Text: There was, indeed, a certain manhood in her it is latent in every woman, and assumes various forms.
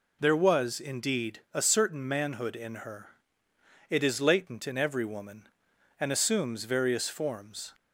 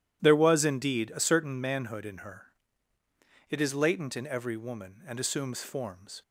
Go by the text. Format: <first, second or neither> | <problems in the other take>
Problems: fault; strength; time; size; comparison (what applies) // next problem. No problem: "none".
first | pauses between "her" and "it"; at 2.4 s; 1.0 s long; noticeable in the first // skips "various"; at 5.6 s